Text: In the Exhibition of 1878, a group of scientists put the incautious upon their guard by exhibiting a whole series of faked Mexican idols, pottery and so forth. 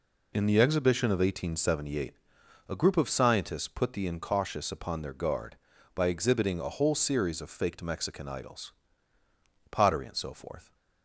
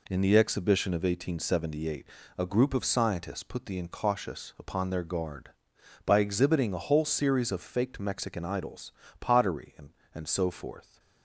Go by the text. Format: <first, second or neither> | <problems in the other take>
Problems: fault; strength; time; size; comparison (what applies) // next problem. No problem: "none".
first | says "and" twice; at 10.1 s